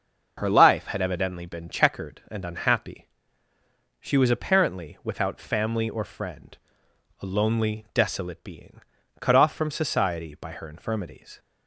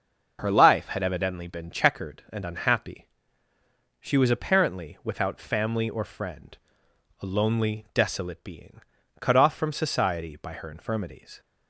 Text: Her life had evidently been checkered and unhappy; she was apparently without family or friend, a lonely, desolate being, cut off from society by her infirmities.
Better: neither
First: starts louder than the rest; noticeable; until 1.3 s; 6 dB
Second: starts louder than the rest; noticeable; until 1.4 s; 6 dB

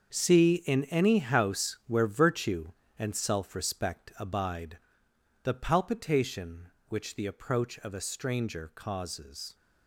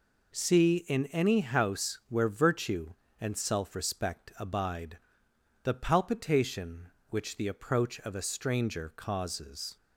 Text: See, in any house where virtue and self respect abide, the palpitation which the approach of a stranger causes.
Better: second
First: gets quieter; strong; throughout; 12 dB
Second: none

